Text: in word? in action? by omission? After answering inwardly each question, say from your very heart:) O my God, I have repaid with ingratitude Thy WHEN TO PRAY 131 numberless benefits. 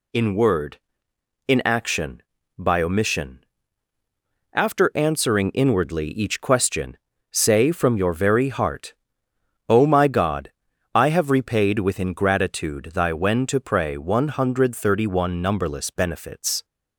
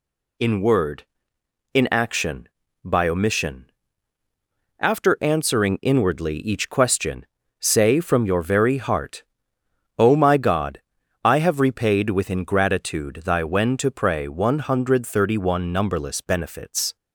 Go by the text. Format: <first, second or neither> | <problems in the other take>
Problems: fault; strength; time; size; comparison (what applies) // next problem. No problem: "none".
neither | none